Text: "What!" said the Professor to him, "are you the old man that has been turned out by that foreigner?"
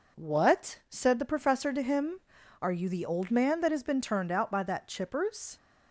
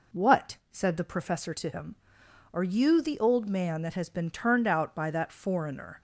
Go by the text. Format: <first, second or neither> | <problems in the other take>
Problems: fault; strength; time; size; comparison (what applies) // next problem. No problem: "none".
second | says "chippers" for "foreigner"; at 4.8 s